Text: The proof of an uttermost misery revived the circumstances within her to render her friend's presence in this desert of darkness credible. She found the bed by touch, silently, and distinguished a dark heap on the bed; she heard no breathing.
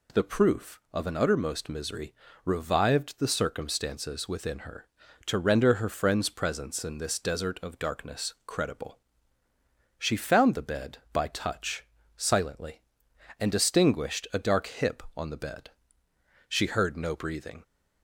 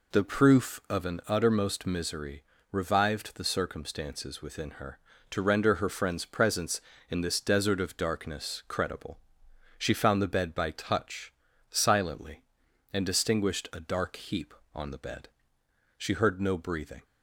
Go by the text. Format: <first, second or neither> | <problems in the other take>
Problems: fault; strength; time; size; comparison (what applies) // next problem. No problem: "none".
second | pauses between "misery" and "revived"; slight; at 2.1 s; 0.32 s long; slight in the second // says "hip" for "heap"; at 14.6 s